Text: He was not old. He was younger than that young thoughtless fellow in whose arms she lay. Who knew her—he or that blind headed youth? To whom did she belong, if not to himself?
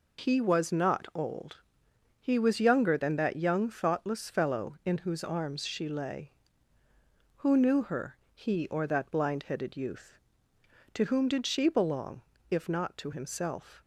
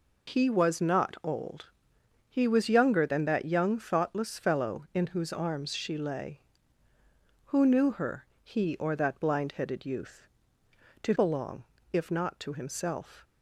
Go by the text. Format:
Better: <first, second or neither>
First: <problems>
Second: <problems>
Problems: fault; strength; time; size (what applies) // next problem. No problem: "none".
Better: first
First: none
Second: skips "whom did she"; at 11.1 s